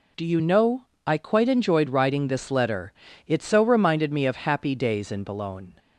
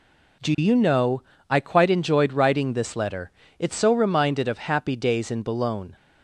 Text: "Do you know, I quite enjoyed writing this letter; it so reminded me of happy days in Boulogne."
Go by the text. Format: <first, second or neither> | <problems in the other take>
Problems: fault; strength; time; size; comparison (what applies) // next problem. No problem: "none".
first | skips "me"; at 4.4 s